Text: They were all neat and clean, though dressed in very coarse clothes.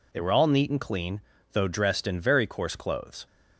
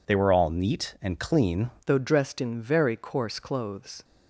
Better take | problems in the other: first | changes voice at "though"; from 1.8 s on; 2.2 s long

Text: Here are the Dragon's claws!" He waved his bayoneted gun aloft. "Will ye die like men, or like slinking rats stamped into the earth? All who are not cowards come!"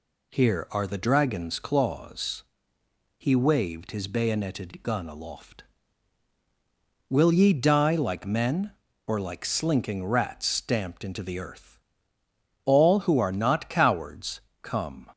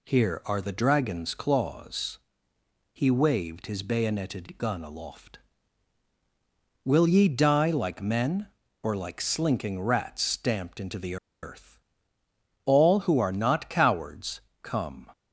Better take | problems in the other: first | pauses between "the" and "earth"; slight; at 11.1 s; 0.27 s long // pauses between "cowards" and "come"; slight; at 14.4 s; 0.20 s long; slight in the first

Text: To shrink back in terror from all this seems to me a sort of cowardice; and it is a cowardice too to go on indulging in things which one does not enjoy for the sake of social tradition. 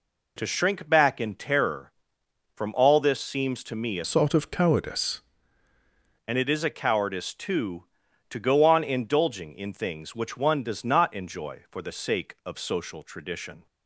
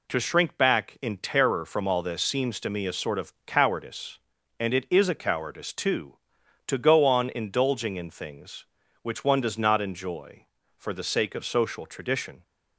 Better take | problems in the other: second | changes voice from "sort" to "cowardice"; from 4.0 to 5.2 s; 1.2 s long

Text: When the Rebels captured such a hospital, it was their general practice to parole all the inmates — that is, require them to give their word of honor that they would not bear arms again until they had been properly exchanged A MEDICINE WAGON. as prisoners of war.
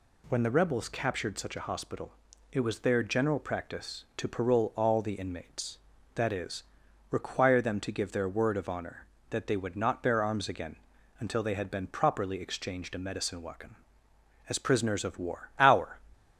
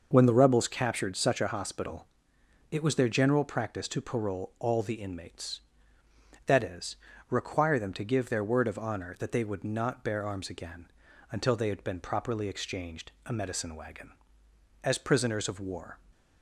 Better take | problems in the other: second | pauses between "again" and "until"; at 10.7 s; 0.42 s long; also in the second // goes on to say "Our"; slight; from 15.5 s on; 0.40 s long

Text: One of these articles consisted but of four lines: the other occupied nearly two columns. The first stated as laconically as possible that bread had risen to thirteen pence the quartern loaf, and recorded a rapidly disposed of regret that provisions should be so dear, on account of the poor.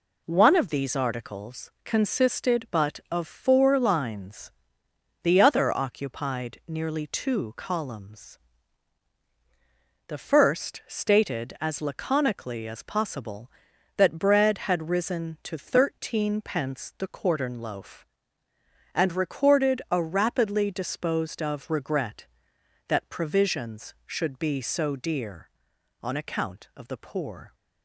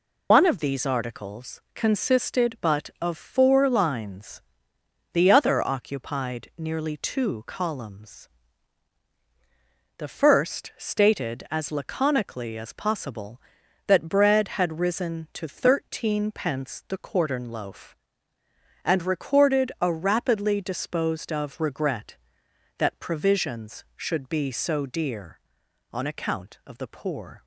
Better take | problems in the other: first | loses the start of "One"; at 0.3 s; 140 ms

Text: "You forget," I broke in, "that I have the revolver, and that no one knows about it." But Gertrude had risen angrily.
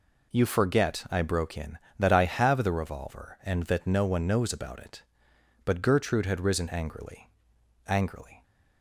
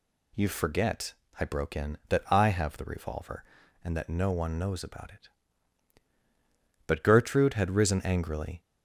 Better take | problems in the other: second | says "angrily" twice; at 7.8 s

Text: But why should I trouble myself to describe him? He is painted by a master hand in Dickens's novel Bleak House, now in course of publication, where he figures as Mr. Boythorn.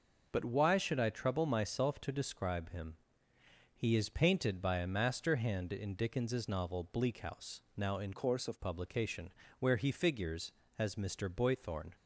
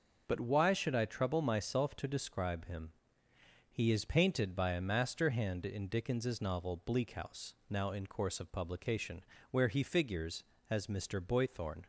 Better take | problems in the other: second | changes voice from "course" to "of"; from 8.1 to 8.6 s; 0.5 s long

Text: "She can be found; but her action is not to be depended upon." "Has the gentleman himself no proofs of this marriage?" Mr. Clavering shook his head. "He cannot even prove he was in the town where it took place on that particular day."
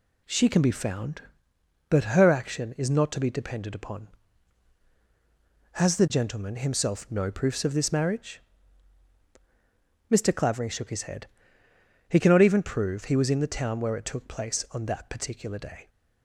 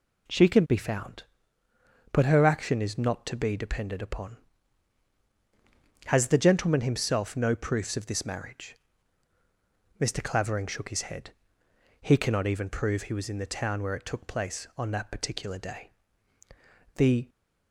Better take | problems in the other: first | goes on to say "The"; slight; from 16.9 s on; 0.32 s long

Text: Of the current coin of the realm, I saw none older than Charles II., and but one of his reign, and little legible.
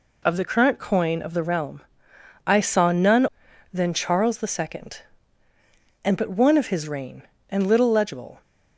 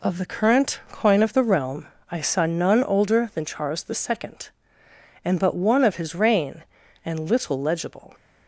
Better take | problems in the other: second | skips "older"; at 3.4 s

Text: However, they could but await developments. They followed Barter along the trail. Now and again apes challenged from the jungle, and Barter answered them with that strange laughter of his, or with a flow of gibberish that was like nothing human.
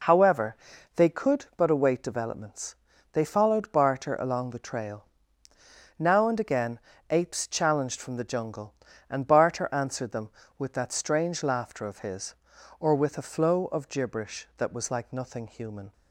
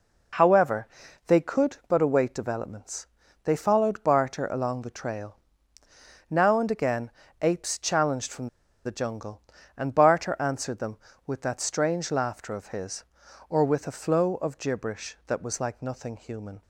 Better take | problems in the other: first | pauses between "again" and "apes"; slight; at 7.1 s; 0.28 s long; slight in the first // pauses between "from" and "the"; at 8.4 s; 0.37 s long

